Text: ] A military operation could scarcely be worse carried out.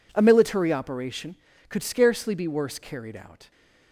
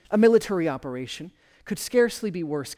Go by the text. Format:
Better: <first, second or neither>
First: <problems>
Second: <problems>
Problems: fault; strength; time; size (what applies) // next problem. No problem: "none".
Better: first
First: none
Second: stops before "carried out"; at 2.7 s